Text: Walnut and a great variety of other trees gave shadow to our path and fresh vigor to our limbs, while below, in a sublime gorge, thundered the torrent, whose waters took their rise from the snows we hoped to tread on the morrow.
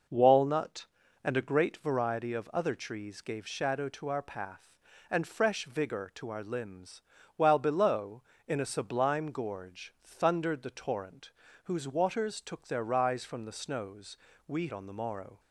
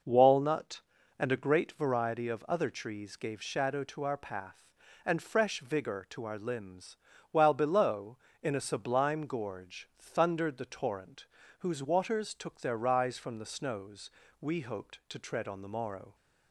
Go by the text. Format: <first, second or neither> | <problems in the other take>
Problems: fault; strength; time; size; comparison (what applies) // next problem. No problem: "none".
second | pauses between "snows" and "we"; slight; at 14.1 s; 0.32 s long; slight in the second // skips "hoped to tread"; at 14.6 s